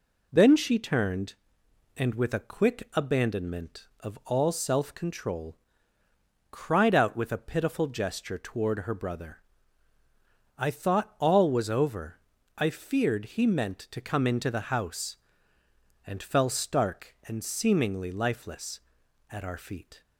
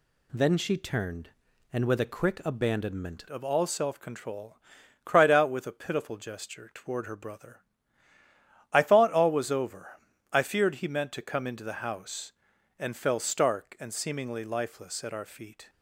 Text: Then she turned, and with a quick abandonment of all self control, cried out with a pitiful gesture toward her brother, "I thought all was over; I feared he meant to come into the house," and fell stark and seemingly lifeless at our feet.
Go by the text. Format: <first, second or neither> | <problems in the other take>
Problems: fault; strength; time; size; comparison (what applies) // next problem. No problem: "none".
first | changes voice at "of"; from 3.2 s on; 12.4 s long